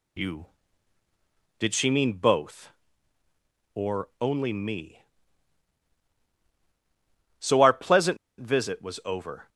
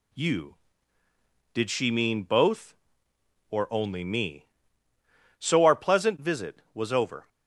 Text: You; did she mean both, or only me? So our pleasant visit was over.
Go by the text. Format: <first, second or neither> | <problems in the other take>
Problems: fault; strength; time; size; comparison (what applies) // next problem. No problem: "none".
second | pauses between "pleasant" and "visit"; slight; at 8.1 s; 0.21 s long